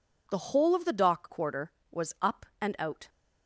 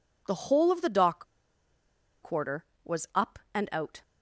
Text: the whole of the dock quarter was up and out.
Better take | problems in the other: first | pauses between "dock" and "quarter"; at 1.2 s; 0.98 s long

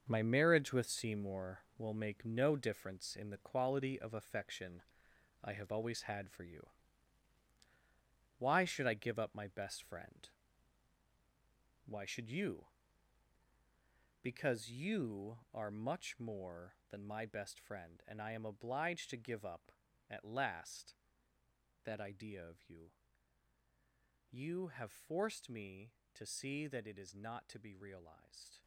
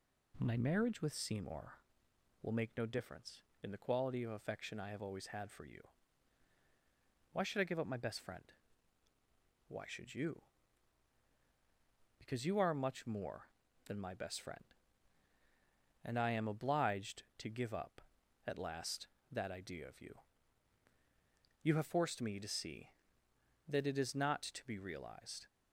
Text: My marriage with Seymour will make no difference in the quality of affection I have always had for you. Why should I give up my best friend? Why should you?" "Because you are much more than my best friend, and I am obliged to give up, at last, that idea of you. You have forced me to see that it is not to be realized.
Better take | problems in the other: second | gets quieter; strong; throughout; 9.5 dB // pauses between "affection" and "I"; noticeable; at 4.8 s; 0.62 s long

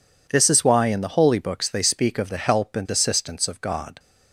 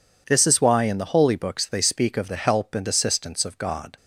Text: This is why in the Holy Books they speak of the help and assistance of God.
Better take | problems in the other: neither | none

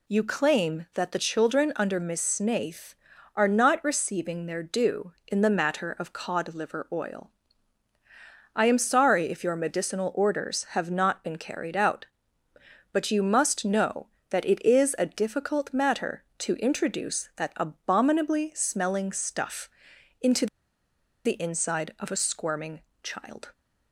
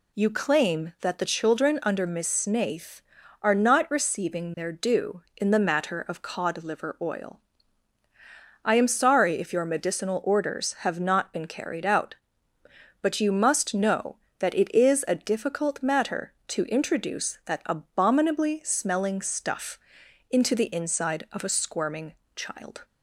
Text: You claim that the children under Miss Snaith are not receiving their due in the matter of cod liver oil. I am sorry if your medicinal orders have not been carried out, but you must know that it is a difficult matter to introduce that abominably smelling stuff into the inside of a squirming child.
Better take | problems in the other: second | pauses between "stuff" and "into"; noticeable; at 19.6 s; 0.50 s long; noticeable in the second // pauses between "into" and "the"; noticeable; at 20.4 s; 0.79 s long // pauses between "squirming" and "child"; slight; at 22.8 s; 0.22 s long; slight in the second

